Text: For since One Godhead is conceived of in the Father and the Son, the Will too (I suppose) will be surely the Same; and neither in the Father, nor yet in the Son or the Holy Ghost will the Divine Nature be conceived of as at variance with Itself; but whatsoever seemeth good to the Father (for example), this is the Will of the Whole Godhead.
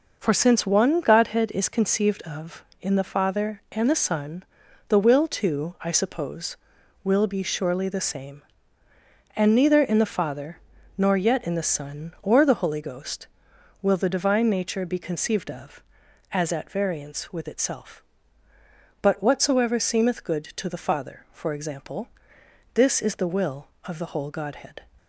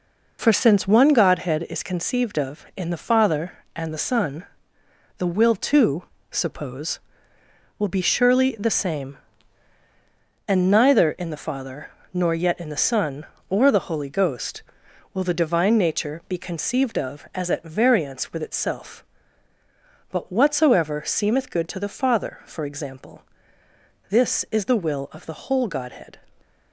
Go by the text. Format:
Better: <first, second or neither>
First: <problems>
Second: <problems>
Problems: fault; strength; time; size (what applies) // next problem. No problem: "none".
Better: first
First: none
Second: skips "I"; at 6.1 s